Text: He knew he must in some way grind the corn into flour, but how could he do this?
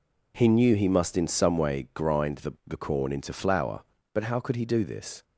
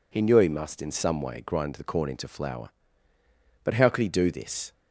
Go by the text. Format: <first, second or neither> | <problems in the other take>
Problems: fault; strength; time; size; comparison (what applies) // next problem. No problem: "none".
second | says "the" twice; at 2.6 s